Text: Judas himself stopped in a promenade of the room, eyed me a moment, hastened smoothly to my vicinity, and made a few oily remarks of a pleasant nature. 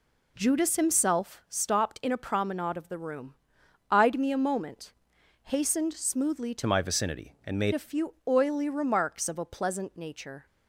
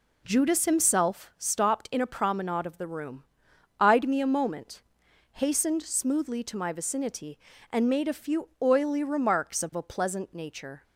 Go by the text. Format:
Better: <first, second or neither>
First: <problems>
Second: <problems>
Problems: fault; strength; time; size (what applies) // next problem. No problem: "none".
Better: second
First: changes voice from "my" to "made"; from 6.6 to 7.7 s; 1.1 s long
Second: none